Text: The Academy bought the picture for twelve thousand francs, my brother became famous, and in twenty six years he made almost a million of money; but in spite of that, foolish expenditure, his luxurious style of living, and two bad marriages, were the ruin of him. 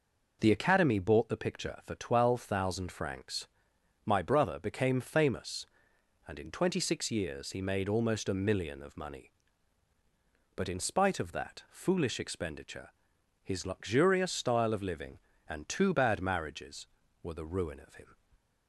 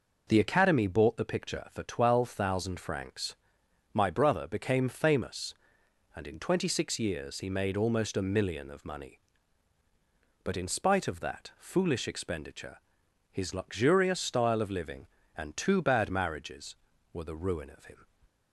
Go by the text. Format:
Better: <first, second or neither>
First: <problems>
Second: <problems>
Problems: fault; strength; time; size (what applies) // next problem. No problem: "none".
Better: neither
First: none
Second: none